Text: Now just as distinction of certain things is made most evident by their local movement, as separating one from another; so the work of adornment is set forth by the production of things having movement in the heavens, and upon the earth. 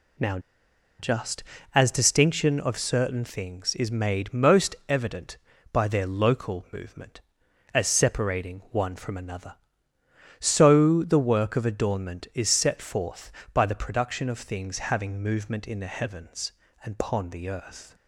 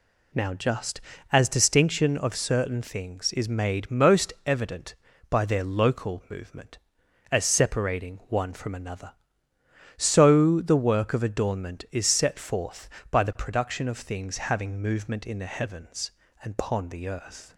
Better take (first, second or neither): second